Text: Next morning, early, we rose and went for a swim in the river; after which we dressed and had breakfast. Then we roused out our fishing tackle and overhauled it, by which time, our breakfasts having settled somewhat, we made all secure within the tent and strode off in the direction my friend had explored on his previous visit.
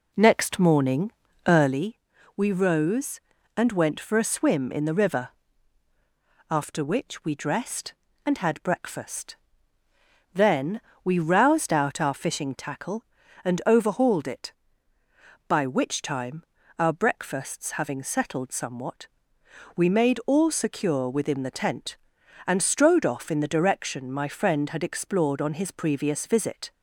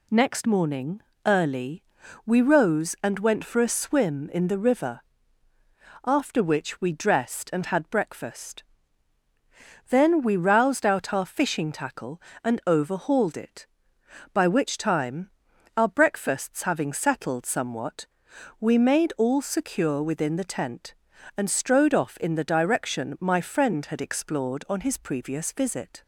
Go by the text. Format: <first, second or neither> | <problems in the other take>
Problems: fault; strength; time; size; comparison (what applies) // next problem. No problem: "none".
second | starts louder than the rest; until 1.8 s; 3.5 dB // pauses between "Then" and "we"; slight; at 10.8 s; 0.22 s long